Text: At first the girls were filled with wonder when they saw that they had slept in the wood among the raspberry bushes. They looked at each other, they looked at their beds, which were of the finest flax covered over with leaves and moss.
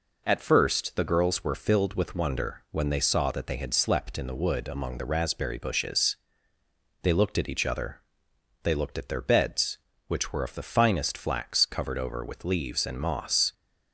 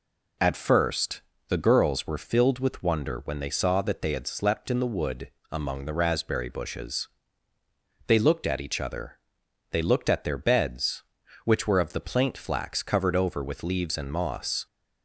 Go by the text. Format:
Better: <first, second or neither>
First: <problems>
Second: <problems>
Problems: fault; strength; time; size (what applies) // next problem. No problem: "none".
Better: first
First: none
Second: pauses between "first" and "the"; slight; at 1.2 s; 0.26 s long // pauses between "wood" and "among"; slight; at 5.2 s; 0.22 s long // says "plaint" for "finest"; at 11.9 s